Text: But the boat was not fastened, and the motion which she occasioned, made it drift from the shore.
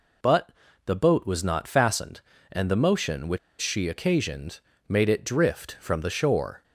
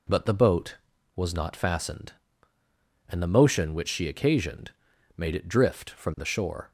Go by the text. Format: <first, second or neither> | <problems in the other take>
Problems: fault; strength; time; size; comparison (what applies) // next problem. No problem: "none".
second | pauses between "But" and "the"; slight; at 0.5 s; 0.34 s long // pauses between "which" and "she"; slight; at 3.3 s; 0.22 s long